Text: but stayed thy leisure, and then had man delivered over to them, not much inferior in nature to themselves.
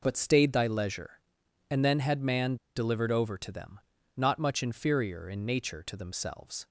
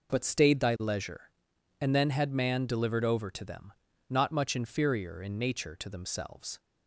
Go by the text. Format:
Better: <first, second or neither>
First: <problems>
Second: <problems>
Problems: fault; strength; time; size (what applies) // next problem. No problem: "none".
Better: second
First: pauses between "man" and "delivered"; slight; at 2.5 s; 0.20 s long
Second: none